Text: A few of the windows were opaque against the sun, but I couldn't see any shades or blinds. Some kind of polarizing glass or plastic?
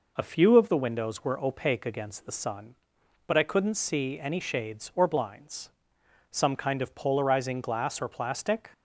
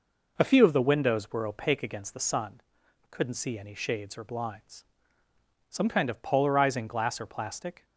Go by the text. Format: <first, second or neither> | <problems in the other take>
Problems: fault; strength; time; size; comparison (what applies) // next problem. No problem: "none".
first | skips "but I"; at 2.8 s